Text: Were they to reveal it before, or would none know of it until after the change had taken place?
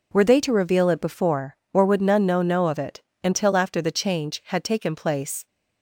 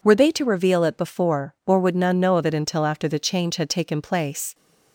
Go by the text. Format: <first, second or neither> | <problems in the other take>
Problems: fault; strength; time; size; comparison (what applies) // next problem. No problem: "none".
second | says "know" twice; at 2.4 s // pauses between "it" and "until"; slight; at 2.9 s; 0.22 s long